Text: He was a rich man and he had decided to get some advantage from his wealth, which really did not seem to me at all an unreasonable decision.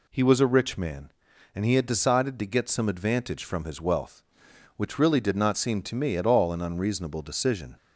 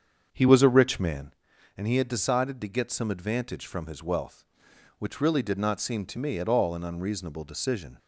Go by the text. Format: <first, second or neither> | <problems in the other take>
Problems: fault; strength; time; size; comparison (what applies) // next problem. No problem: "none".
first | starts louder than the rest; until 1.3 s; 7 dB